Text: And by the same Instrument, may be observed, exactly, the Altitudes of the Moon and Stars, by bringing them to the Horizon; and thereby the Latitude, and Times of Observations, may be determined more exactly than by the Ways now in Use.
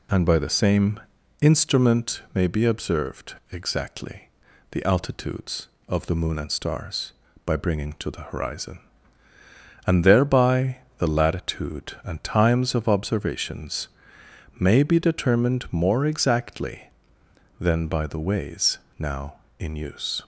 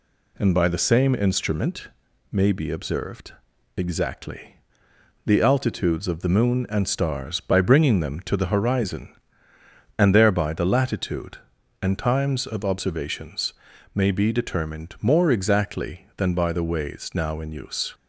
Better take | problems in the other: second | pauses between "same" and "Instrument"; at 1.0 s; 0.40 s long // skips "them"; at 7.9 s // pauses between "thereby" and "the"; slight; at 10.8 s; 0.18 s long // pauses between "Ways" and "now"; slight; at 18.7 s; 0.20 s long

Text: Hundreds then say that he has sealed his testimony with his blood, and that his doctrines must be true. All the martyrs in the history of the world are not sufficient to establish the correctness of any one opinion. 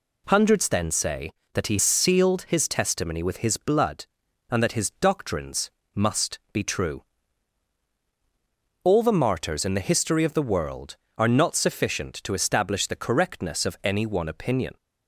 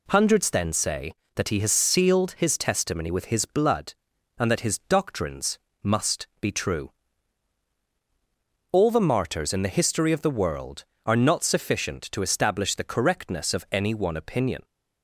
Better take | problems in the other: second | skips "has"; at 1.8 s // pauses between "doctrines" and "must"; slight; at 5.6 s; 0.24 s long; slight in the second

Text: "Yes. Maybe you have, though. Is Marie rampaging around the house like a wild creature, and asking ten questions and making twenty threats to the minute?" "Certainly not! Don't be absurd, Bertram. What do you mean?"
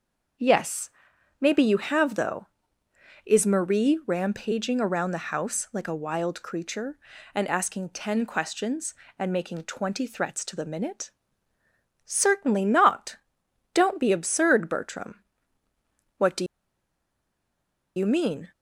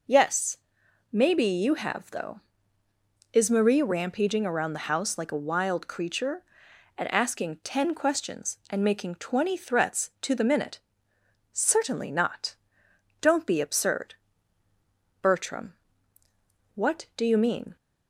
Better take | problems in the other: second | starts louder than the rest; until 1.8 s; 6 dB // pauses between "do" and "you"; strong; at 16.4 s; 1.5 s long

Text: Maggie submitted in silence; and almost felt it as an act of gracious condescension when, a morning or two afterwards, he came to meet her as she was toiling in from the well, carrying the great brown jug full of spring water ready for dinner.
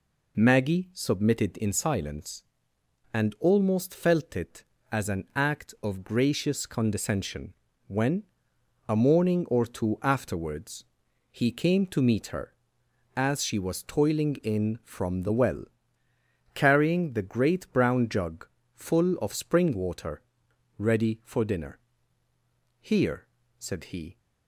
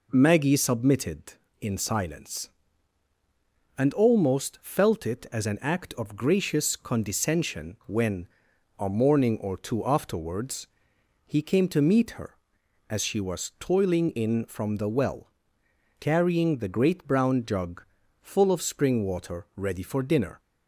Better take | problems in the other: second | pauses between "condescension" and "when"; slight; at 7.5 s; 0.34 s long // pauses between "jug" and "full"; slight; at 18.4 s; 0.28 s long; slight in the second // pauses between "water" and "ready"; noticeable; at 20.1 s; 0.58 s long // goes on to say "Here said he"; from 22.8 s on; 1.3 s long

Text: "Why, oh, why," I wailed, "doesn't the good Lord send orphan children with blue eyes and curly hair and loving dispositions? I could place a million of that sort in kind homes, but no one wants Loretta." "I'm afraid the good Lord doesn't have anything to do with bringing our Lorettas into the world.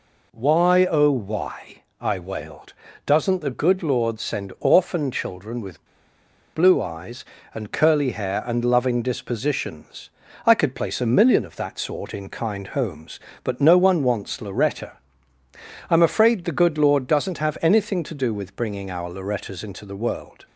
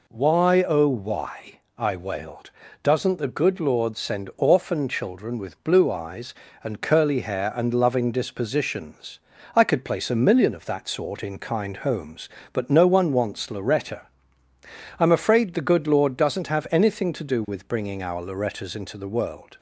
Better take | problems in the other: second | pauses between "with" and "blue"; noticeable; at 5.8 s; 0.70 s long

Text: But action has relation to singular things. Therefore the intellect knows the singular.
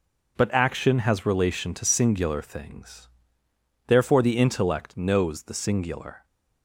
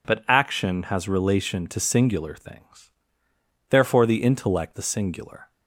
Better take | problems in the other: first | skips "knows"; at 4.7 s

